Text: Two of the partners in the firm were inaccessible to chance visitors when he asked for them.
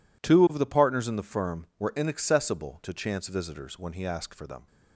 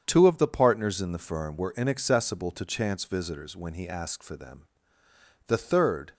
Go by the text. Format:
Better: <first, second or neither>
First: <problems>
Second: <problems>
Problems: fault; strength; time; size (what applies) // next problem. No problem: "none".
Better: first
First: none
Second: starts louder than the rest; strong; until 1.0 s; 7.5 dB // goes on to say "The third"; noticeable; from 5.4 s on; 0.66 s long